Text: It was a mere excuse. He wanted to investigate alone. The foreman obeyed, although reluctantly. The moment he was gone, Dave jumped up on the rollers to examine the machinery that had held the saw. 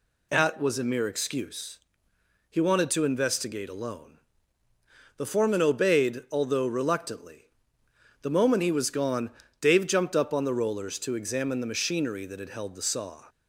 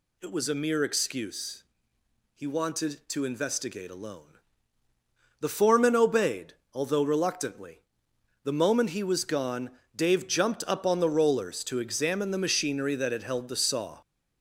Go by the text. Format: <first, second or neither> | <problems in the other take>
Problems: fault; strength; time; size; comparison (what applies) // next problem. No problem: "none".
second | says "At" for "It"; at 0.3 s